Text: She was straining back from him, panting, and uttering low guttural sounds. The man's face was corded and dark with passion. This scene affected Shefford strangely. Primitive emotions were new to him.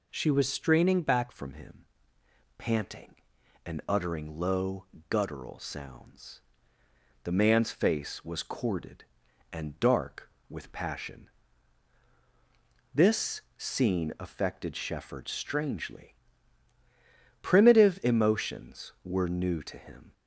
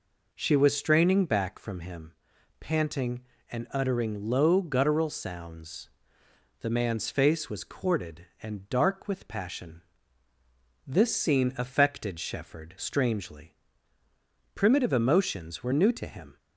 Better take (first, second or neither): second